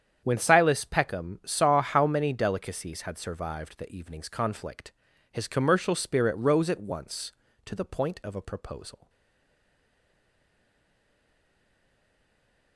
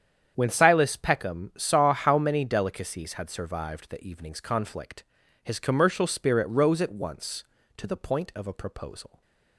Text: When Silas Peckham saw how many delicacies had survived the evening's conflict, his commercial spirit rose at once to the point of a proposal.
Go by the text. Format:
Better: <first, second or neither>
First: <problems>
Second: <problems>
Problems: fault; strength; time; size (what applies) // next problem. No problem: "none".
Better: second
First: starts louder than the rest; strong; until 1.2 s; 8.5 dB // stays silent after the last word; strong; from 9.0 s on; 3.7 s long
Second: starts louder than the rest; strong; until 1.3 s; 8.5 dB